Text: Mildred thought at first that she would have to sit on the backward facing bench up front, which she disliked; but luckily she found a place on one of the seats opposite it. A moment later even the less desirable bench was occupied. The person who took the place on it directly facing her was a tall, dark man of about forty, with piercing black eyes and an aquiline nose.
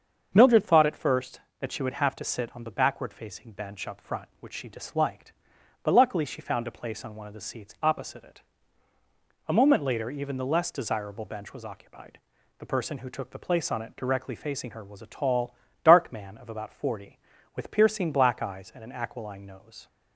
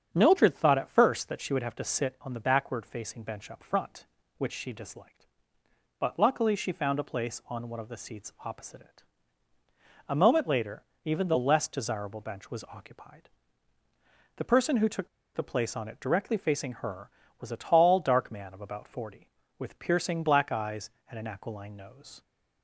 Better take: first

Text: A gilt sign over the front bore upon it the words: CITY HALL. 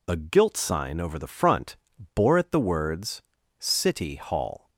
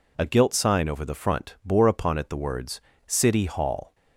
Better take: second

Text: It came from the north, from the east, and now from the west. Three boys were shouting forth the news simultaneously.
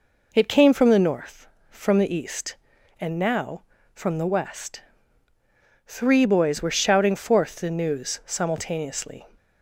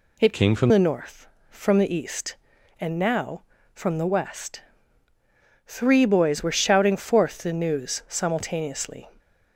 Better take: first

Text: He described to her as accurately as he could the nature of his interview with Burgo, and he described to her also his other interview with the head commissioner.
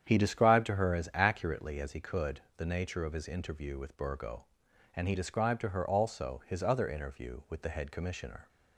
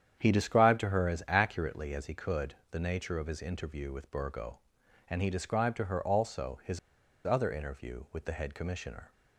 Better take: first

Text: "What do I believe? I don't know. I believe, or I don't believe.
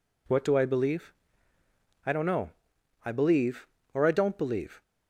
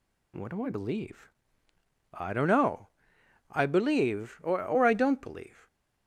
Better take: first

